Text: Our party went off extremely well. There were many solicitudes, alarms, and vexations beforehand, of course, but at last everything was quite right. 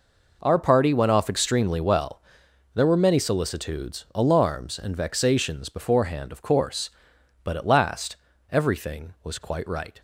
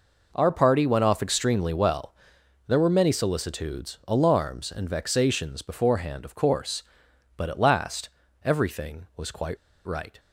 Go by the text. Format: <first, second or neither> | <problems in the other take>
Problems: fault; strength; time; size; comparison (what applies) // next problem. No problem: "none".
first | pauses between "last" and "everything"; slight; at 8.0 s; 0.36 s long; slight in the first // pauses between "quite" and "right"; slight; at 9.5 s; 0.29 s long